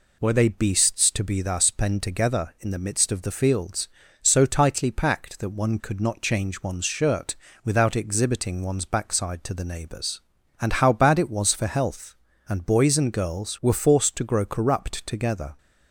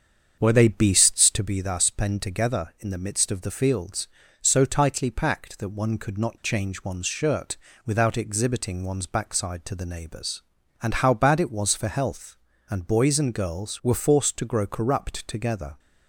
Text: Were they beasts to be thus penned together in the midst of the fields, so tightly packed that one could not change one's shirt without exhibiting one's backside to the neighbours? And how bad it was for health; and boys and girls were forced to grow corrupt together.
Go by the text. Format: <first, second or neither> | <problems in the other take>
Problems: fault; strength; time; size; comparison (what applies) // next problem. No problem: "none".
first | starts louder than the rest; strong; until 1.5 s; 7 dB // pauses between "shirt" and "without"; slight; at 7.5 s; 0.28 s long; slight in the first